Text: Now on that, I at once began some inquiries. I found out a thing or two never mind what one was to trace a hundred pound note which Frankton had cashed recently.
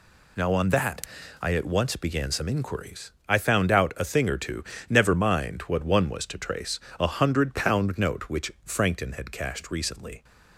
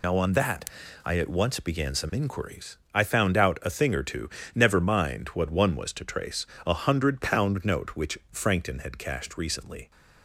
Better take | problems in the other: first | loses the start of "Now"; at 0.0 s; 35 ms // pauses between "two" and "never"; slight; at 4.2 s; 0.26 s long; slight in the first // pauses between "trace" and "a"; slight; at 6.4 s; 0.20 s long; slight in the first

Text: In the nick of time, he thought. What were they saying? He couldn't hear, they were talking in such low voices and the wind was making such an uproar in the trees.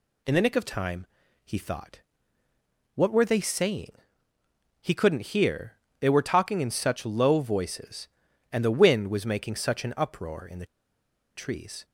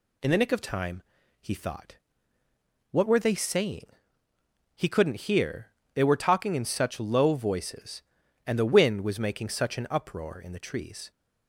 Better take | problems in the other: second | pauses between "the" and "trees"; noticeable; at 10.6 s; 0.70 s long

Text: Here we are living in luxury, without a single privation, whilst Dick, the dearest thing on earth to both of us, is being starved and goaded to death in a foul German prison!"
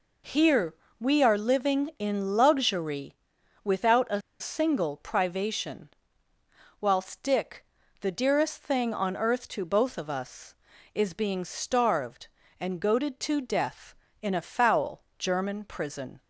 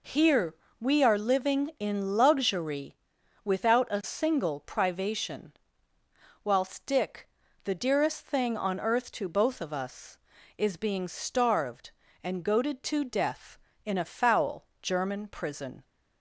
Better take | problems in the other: second | pauses between "Here" and "we"; slight; at 0.7 s; 0.26 s long; slight in the second // pauses between "a" and "single"; slight; at 4.2 s; 0.20 s long // pauses between "foul" and "German"; slight; at 14.9 s; 0.18 s long; slight in the second

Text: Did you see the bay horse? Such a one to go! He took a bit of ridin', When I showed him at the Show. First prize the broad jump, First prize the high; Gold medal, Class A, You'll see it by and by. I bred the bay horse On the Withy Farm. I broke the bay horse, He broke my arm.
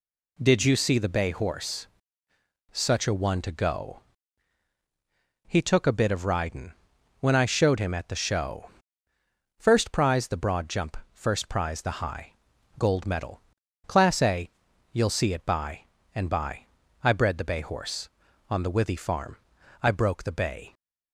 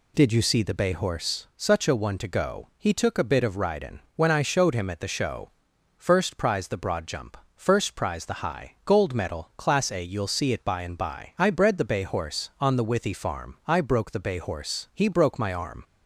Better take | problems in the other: second | stops before "horse He broke my arm"; at 20.7 s

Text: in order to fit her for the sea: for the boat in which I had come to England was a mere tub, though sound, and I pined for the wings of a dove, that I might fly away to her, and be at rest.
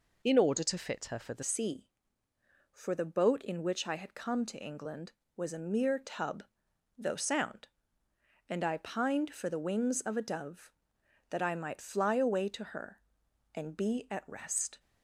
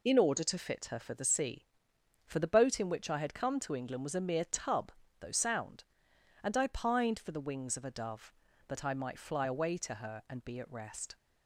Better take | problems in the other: second | changes voice at "sea"; from 1.4 s on; 13.3 s long

